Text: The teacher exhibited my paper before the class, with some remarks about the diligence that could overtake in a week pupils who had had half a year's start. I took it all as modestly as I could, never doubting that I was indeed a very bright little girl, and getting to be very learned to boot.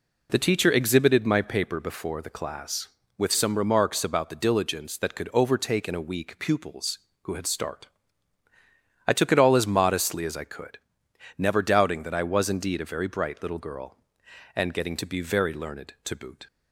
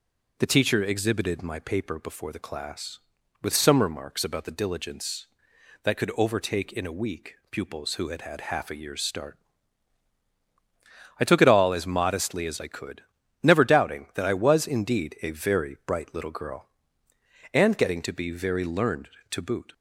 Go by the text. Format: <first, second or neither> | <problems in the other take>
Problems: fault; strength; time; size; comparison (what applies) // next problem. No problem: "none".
second | skips "had half a year's"; at 7.4 s